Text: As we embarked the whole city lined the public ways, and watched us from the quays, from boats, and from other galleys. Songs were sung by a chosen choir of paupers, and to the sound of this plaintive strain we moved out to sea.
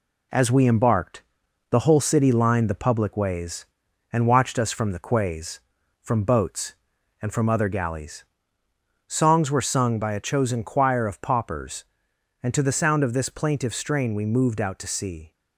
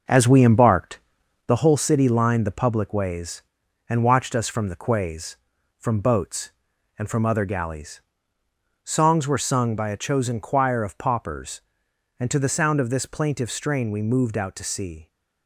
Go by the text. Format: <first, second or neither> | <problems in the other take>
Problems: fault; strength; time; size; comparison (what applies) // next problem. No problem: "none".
first | starts louder than the rest; noticeable; until 1.5 s; 5.5 dB // pauses between "embarked" and "the"; noticeable; at 0.9 s; 0.46 s long; noticeable in the first